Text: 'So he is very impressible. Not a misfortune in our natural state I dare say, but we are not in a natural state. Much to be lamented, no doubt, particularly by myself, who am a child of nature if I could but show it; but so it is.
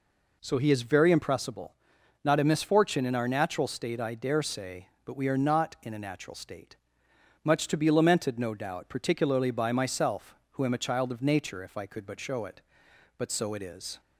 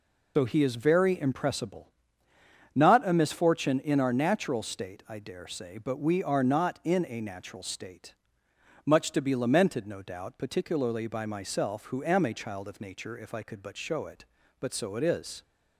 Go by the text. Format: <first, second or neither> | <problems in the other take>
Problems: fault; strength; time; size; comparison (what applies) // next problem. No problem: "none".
first | loses the start of "So"; at 0.3 s; 90 ms